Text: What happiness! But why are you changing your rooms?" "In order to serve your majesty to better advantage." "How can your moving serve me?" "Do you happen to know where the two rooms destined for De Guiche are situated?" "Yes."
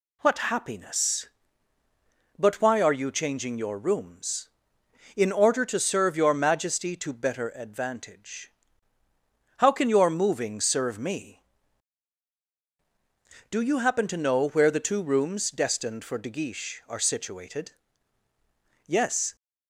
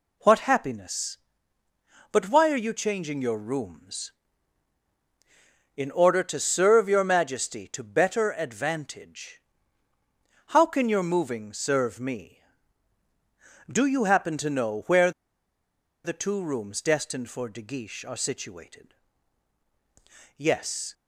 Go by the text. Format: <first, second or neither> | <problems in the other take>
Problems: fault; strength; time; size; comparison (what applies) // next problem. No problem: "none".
first | pauses between "where" and "the"; noticeable; at 15.1 s; 0.92 s long